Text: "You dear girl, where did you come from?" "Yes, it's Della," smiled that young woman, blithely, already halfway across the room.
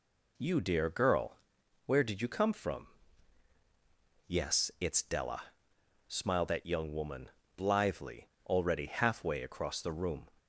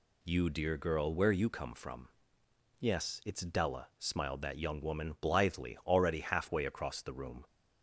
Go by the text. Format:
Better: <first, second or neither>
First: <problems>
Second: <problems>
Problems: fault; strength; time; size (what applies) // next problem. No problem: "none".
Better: first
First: none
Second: skips "did"; at 1.3 s